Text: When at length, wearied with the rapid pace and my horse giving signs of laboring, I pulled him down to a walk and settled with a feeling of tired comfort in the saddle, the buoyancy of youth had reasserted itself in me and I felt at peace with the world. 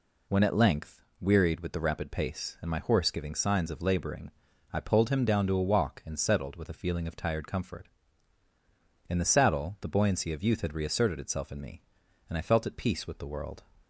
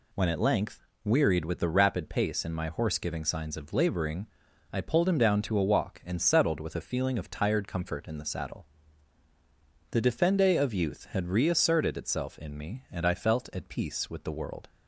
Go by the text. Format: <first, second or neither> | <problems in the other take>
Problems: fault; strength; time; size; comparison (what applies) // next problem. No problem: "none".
first | says "defende" for "buoyancy"; at 10.0 s